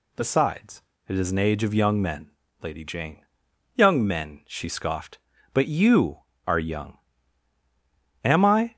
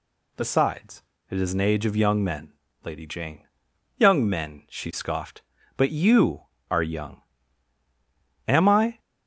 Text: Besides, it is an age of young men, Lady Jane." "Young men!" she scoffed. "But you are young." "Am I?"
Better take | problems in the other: neither | none

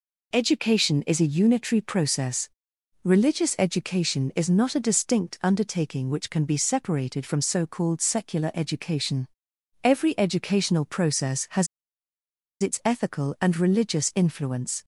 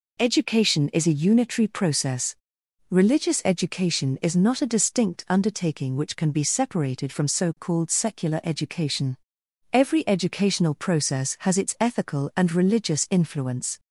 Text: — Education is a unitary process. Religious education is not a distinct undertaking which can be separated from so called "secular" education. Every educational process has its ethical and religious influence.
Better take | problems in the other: second | pauses between "has" and "its"; noticeable; at 11.6 s; 0.94 s long

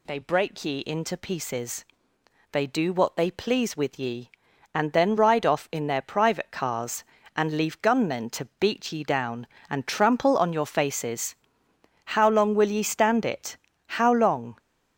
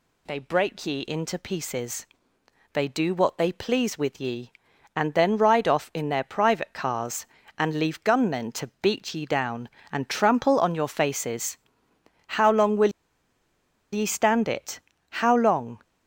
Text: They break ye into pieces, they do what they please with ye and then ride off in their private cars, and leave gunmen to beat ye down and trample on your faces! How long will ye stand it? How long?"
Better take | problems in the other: first | pauses between "will" and "ye"; at 12.9 s; 1.0 s long

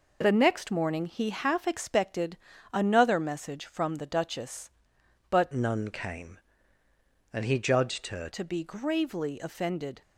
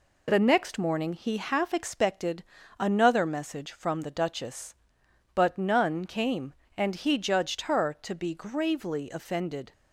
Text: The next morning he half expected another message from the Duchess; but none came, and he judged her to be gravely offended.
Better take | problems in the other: second | pauses between "expected" and "another"; slight; at 2.3 s; 0.34 s long; slight in the second // changes voice from "none" to "her"; from 5.5 to 8.2 s; 2.7 s long

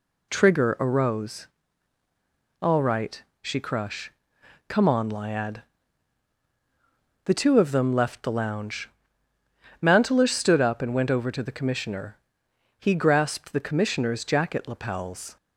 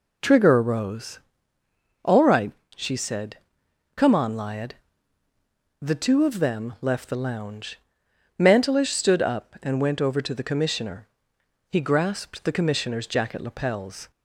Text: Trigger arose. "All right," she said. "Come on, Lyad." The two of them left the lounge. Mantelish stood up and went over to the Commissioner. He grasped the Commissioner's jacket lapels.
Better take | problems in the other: second | says "crush" for "said"; at 3.5 s

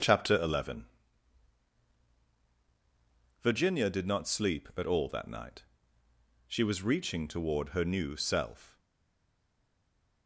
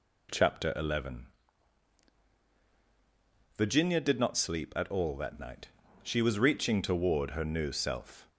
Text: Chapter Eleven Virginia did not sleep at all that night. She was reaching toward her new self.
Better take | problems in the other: second | starts louder than the rest; until 3.5 s; 6.5 dB // pauses between "Eleven" and "Virginia"; strong; at 0.8 s; 2.5 s long; strong in the second // stays silent after the last word; noticeable; from 8.7 s on; 1.5 s long

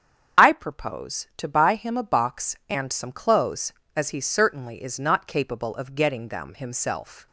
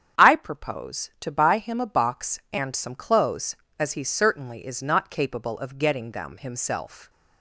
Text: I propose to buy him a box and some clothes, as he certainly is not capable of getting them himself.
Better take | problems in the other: second | loses the start of "I"; at 0.3 s; 35 ms // starts louder than the rest; strong; until 1.5 s; 8 dB; strong in the second

